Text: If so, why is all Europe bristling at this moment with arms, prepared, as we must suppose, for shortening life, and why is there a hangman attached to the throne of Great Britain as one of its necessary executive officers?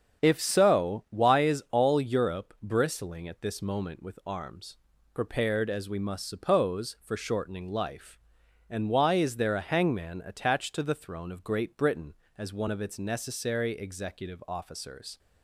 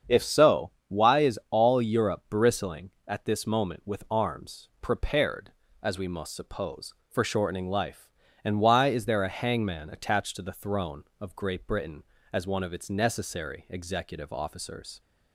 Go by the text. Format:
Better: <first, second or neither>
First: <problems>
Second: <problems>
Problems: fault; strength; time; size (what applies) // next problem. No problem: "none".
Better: neither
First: starts louder than the rest; strong; until 1.2 s; 7.5 dB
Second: starts louder than the rest; strong; until 1.2 s; 7.5 dB